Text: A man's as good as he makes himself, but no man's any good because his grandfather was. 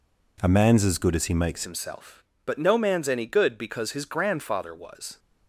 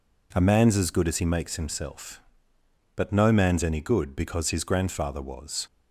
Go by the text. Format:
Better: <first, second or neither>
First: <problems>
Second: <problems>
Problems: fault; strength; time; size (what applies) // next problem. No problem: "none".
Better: second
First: changes voice at "himself"; from 1.6 s on; 3.5 s long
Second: none